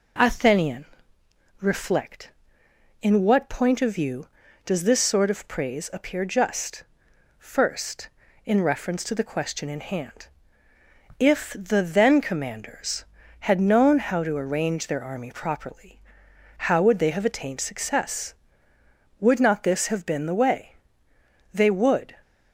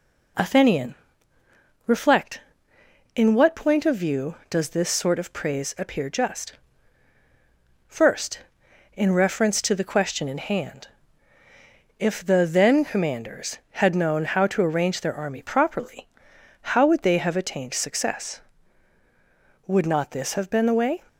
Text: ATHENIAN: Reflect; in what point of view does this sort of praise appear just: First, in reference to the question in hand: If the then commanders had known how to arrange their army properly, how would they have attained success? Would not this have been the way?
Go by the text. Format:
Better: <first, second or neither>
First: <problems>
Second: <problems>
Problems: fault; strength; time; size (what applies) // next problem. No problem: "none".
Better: second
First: goes on to say "They would"; noticeable; from 21.5 s on; 0.62 s long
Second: none